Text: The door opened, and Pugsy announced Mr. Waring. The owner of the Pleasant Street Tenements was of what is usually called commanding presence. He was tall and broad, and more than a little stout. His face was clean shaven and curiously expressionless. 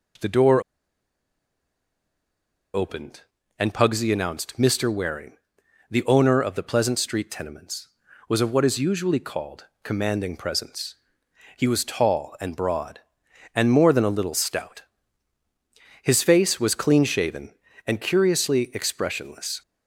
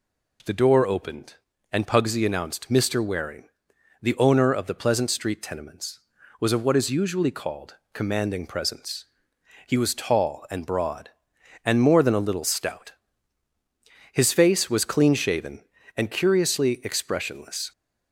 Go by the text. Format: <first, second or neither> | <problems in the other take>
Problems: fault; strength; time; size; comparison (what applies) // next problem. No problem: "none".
second | pauses between "door" and "opened"; strong; at 0.6 s; 2.1 s long // pauses between "called" and "commanding"; slight; at 9.6 s; 0.16 s long; slight in the second